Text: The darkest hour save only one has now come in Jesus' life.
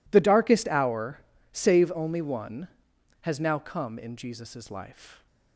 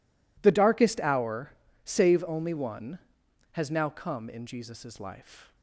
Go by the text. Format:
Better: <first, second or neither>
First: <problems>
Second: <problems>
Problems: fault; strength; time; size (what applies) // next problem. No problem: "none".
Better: neither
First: pauses between "hour" and "save"; slight; at 1.2 s; 0.32 s long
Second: pauses between "hour" and "save"; slight; at 1.5 s; 0.32 s long